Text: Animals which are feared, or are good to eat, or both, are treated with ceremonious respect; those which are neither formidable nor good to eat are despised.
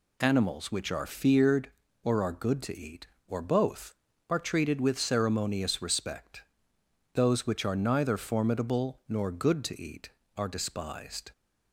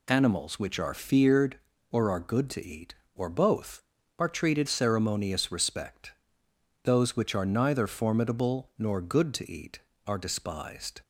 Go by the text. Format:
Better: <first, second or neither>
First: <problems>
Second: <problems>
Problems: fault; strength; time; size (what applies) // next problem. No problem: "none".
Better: first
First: none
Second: skips "with"; at 4.6 s